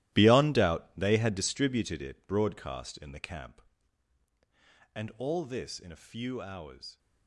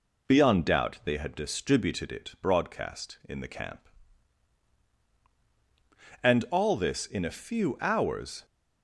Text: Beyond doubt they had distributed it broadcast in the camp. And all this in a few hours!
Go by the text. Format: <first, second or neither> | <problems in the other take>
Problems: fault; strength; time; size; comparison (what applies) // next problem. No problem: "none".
second | gets quieter; strong; throughout; 12.5 dB